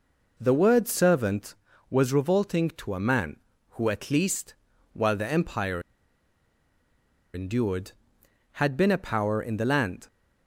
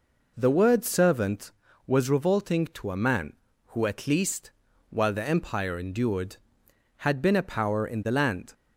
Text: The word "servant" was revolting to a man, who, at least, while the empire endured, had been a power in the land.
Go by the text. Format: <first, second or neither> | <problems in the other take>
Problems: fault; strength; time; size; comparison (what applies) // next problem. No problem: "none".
second | pauses between "empire" and "endured"; strong; at 5.8 s; 1.5 s long